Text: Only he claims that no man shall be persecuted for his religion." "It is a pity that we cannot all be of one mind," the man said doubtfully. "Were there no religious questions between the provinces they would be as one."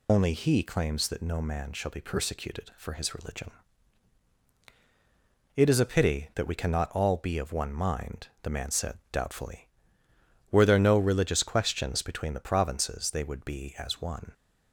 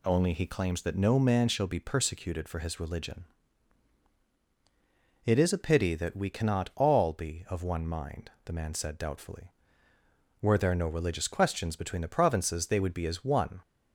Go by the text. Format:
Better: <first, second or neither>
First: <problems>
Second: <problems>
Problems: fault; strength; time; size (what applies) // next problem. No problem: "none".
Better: second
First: loses the start of "Only"; at 0.0 s; 80 ms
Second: none